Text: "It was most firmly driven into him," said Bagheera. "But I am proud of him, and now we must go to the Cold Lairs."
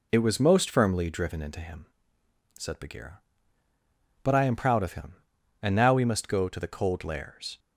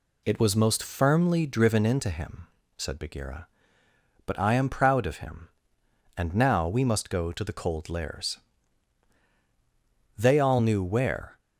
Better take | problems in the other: first | goes on to say "They all knew where"; noticeable; from 10.1 s on; 1.2 s long

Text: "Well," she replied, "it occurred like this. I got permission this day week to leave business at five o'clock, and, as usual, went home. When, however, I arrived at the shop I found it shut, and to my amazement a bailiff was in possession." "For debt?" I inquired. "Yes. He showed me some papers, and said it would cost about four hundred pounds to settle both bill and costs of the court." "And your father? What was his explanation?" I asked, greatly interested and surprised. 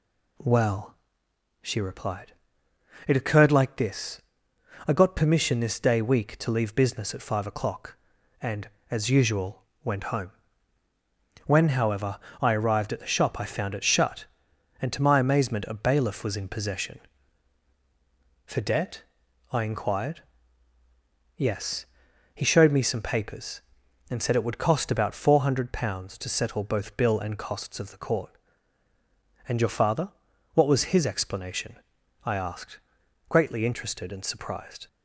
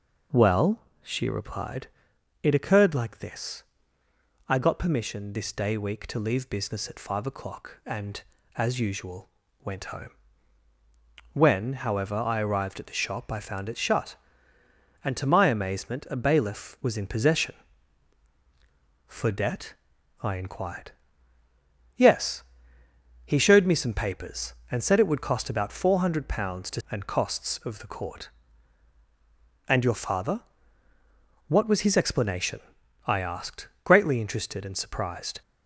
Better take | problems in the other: first | skips "settle both bill"; at 26.8 s

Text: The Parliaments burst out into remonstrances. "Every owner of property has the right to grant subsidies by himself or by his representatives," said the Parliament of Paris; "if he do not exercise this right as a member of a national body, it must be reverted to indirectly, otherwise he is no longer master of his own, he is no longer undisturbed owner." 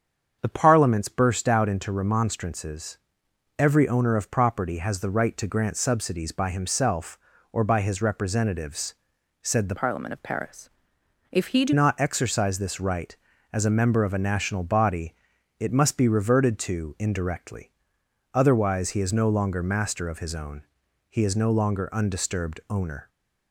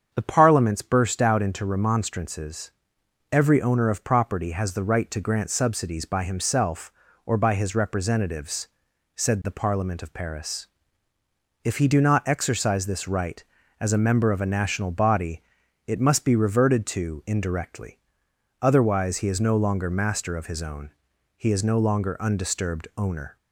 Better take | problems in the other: second | starts louder than the rest; strong; until 1.4 s; 7.5 dB; strong in the second // changes voice from "Parliament" to "do"; from 9.7 to 11.7 s; 2.0 s long

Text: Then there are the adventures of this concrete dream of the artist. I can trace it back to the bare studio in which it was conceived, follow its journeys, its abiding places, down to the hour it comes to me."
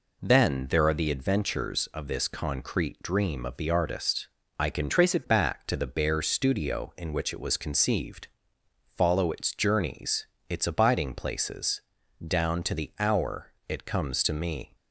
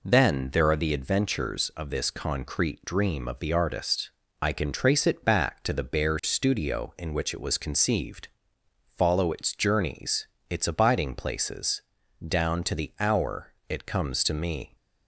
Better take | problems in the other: second | changes voice from "trace" to "it"; from 4.8 to 5.2 s; 0.4 s long

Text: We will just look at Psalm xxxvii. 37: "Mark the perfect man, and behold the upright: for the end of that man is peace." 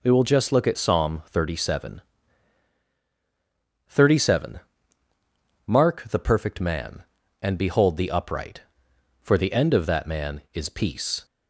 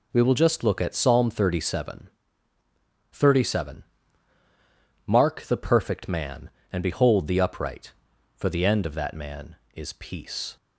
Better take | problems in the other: neither | none

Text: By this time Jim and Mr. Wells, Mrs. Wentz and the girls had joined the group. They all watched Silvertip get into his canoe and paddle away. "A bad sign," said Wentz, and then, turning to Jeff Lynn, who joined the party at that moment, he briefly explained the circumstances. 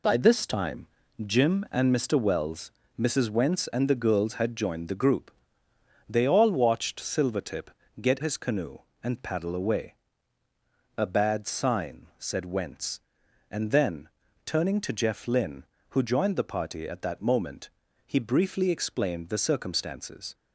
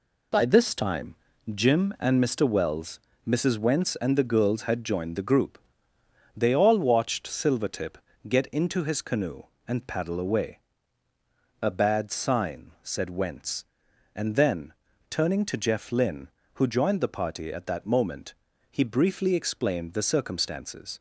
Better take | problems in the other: second | pauses between "time" and "Jim"; at 0.8 s; 0.40 s long; also in the second // pauses between "Silvertip" and "get"; slight; at 7.6 s; 0.30 s long; slight in the second // skips "into"; at 8.1 s

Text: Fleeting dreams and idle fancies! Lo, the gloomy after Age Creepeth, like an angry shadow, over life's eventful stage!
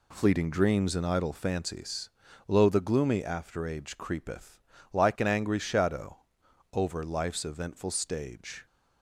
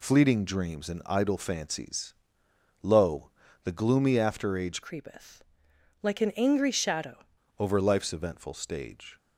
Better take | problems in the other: first | changes voice from "Creepeth" to "shadow"; from 4.8 to 7.2 s; 2.4 s long

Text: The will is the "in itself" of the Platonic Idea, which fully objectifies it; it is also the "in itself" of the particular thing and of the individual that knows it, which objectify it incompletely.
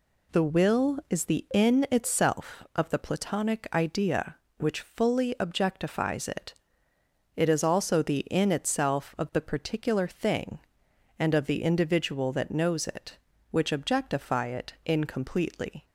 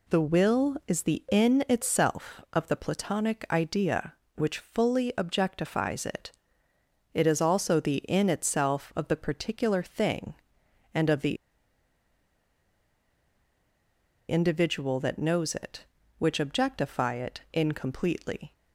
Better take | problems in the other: first | pauses between "the" and "individual"; strong; at 11.3 s; 2.9 s long

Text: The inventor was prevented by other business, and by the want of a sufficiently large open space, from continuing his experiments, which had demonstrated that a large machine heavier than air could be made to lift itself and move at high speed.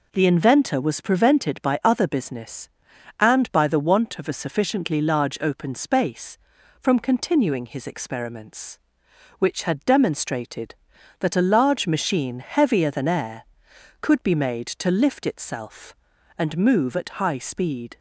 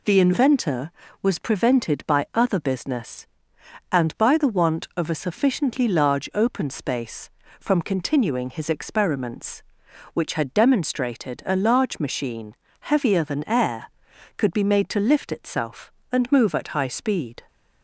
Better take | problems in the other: first | skips "that"; at 11.4 s // pauses between "machine" and "heavier"; slight; at 12.5 s; 0.26 s long

